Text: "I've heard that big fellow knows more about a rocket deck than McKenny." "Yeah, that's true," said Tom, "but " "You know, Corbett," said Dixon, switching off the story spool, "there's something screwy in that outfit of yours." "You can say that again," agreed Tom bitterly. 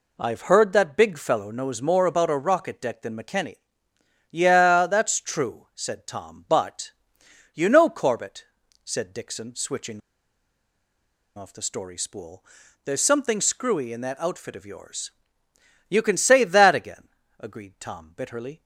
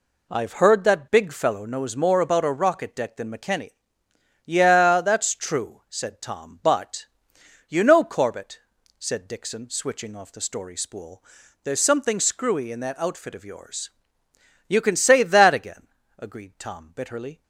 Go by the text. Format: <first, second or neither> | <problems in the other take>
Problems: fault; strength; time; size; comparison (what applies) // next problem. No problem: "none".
second | pauses between "switching" and "off"; strong; at 10.0 s; 1.3 s long